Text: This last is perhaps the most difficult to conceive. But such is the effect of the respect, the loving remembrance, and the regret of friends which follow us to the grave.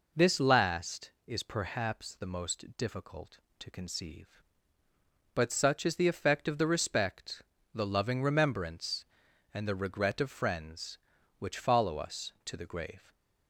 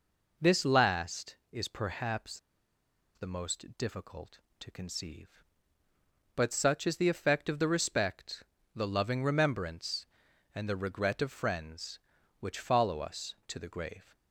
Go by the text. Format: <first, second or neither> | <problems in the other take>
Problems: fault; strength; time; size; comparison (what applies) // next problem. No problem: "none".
first | pauses between "perhaps" and "the"; noticeable; at 2.3 s; 0.77 s long